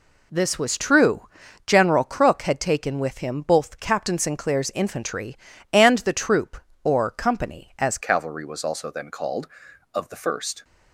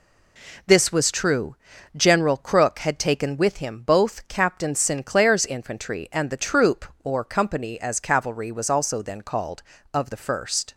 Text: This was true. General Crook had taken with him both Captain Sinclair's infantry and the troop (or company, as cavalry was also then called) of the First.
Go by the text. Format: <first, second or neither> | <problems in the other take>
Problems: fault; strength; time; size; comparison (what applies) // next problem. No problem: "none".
second | changes voice at "cavalry"; from 8.0 s on; 2.6 s long